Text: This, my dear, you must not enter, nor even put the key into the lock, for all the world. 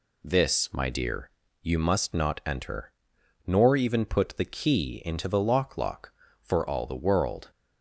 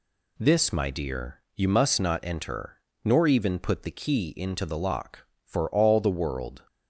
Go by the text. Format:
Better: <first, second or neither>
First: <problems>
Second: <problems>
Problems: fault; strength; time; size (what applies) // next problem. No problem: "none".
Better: second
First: says "lock" twice; at 5.7 s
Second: none